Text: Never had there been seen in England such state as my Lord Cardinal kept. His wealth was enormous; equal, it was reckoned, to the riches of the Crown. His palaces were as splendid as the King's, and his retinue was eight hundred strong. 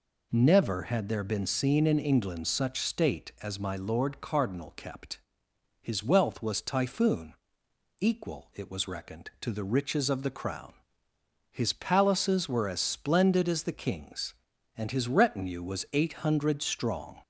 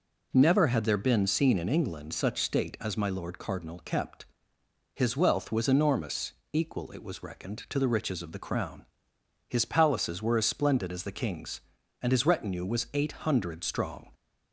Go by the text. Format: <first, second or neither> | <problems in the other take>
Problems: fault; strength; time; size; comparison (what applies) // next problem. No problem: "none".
second | says "typhoon" for "enormous"; at 6.5 s